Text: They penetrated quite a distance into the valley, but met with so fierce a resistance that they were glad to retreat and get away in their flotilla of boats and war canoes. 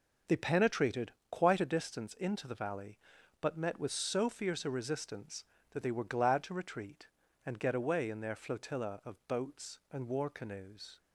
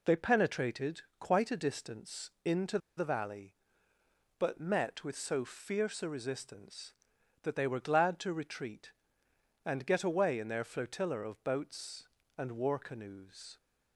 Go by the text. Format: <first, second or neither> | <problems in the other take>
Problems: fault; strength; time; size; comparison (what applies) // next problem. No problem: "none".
first | pauses between "penetrated" and "quite"; slight; at 1.0 s; 0.18 s long; slight in the first // pauses between "into" and "the"; slight; at 2.7 s; 0.19 s long